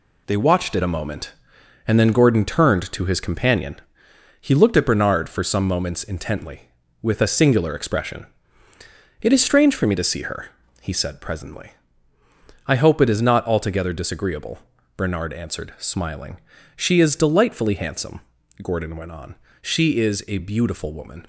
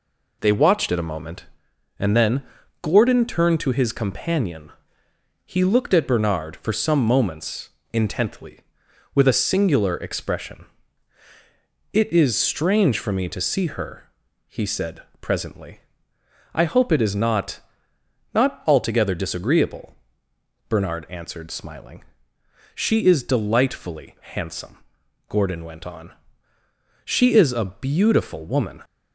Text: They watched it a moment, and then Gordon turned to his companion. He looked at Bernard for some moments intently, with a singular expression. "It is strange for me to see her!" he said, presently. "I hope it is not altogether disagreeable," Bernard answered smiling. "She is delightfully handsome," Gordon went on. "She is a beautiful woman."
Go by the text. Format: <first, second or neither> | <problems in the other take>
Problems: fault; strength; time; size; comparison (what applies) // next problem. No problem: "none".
first | pauses between "then" and "Gordon"; at 2.4 s; 0.40 s long // pauses between "moments" and "intently"; slight; at 7.7 s; 0.22 s long // says "not" twice; at 18.3 s // pauses between "delightfully" and "handsome"; slight; at 24.1 s; 0.20 s long